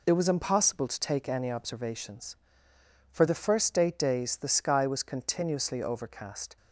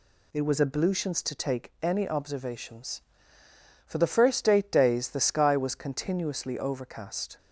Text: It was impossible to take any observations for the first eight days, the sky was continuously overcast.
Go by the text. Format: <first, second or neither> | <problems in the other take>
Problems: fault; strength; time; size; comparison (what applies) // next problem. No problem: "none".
first | says "ablutions" for "impossible"; at 0.6 s